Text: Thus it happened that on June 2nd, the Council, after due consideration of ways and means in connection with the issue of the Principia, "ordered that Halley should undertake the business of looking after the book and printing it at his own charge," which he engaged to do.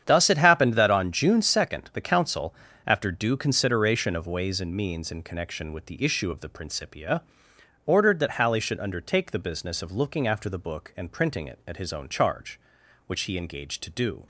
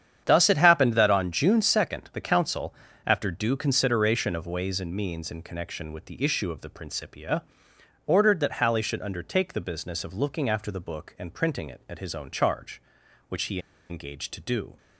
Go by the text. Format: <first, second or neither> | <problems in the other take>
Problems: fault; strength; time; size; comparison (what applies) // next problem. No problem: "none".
first | starts louder than the rest; strong; until 1.2 s; 9 dB; strong in the first // pauses between "he" and "engaged"; slight; at 13.5 s; 0.31 s long